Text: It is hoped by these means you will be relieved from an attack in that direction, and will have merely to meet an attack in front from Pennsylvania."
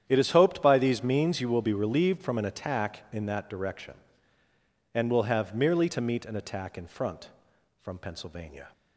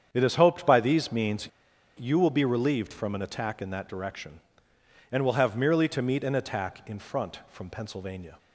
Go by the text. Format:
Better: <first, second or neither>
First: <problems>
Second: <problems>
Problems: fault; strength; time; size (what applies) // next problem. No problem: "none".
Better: first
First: starts louder than the rest; strong; until 1.0 s; 9.5 dB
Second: starts louder than the rest; strong; until 1.1 s; 8 dB // pauses between "means" and "you"; noticeable; at 1.4 s; 0.48 s long